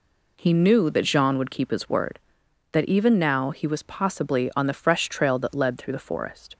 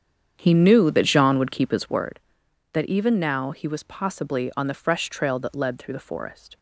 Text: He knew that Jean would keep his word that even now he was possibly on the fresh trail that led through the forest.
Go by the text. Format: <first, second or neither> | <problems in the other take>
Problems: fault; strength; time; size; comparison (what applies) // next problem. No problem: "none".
first | starts louder than the rest; strong; until 2.1 s; 8 dB